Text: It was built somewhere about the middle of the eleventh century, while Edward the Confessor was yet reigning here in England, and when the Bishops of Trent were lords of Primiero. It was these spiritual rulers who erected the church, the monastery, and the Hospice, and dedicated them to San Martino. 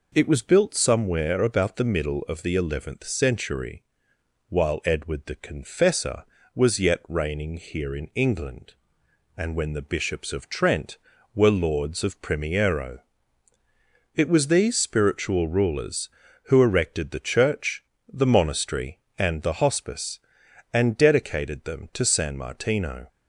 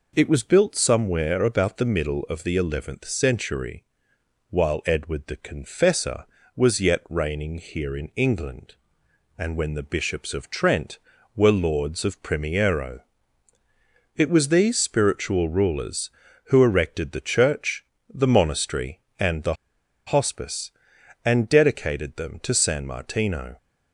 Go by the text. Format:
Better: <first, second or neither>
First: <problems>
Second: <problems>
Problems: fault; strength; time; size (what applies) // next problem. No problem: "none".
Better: first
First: none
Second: pauses between "the" and "Hospice"; noticeable; at 19.5 s; 0.52 s long